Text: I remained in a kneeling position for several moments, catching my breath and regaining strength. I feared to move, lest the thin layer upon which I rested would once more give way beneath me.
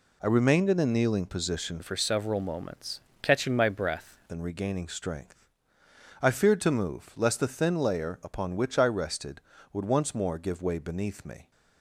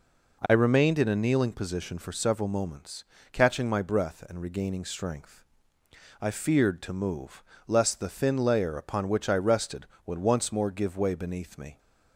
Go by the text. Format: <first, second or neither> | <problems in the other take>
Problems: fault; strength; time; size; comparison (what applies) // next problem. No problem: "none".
second | changes voice from "for" to "breath"; from 1.8 to 4.0 s; 2.2 s long